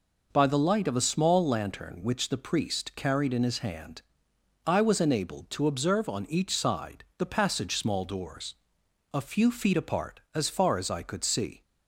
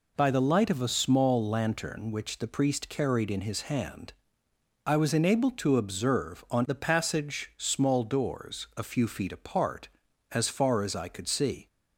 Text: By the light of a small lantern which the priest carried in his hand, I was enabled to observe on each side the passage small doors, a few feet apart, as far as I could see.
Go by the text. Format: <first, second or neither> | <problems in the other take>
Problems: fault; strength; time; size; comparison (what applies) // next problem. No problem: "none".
first | skips "each side"; at 6.6 s